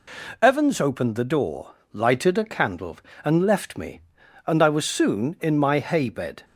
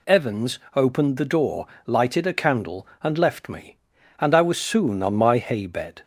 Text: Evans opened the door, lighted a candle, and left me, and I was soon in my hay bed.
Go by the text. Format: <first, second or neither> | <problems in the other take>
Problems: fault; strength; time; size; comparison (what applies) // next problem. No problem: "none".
first | pauses between "Evans" and "opened"; slight; at 0.5 s; 0.18 s long // says "on" for "in"; at 5.0 s